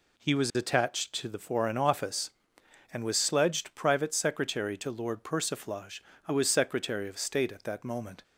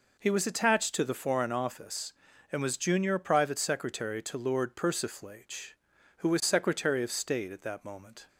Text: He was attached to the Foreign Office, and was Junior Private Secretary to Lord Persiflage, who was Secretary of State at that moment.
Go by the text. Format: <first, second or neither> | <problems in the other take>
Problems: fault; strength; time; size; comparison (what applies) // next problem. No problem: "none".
second | says "Sledged" for "Junior"; at 3.1 s